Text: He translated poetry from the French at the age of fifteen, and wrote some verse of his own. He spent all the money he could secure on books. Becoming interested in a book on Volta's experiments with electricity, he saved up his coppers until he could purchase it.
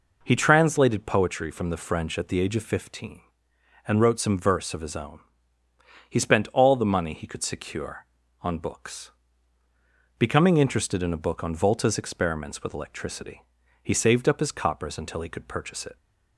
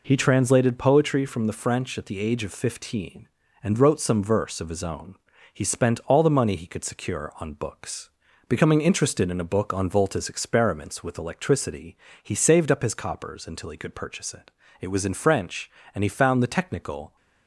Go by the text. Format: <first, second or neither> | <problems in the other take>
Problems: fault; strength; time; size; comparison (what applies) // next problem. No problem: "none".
first | goes on to say "It was in French and he found the technical"; strong; from 14.7 s on; 2.3 s long